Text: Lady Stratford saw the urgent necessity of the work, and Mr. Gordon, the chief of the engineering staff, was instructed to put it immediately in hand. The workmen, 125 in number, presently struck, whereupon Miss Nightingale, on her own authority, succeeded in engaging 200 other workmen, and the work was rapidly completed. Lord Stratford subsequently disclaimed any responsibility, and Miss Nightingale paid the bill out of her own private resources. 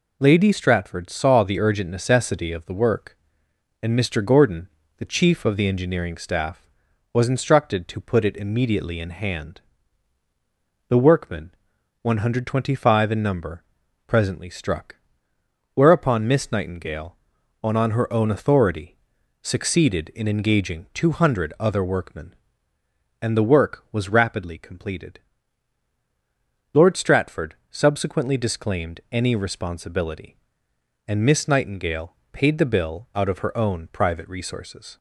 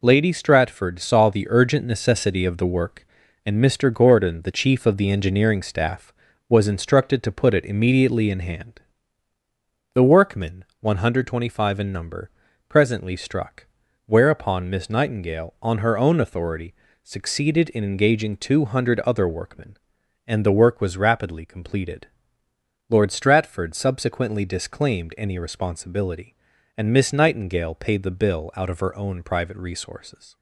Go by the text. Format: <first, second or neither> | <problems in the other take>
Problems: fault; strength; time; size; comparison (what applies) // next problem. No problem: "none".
second | says "on" twice; at 17.7 s // pauses between "Stratford" and "subsequently"; slight; at 27.5 s; 0.16 s long // pauses between "Nightingale" and "paid"; slight; at 32.1 s; 0.20 s long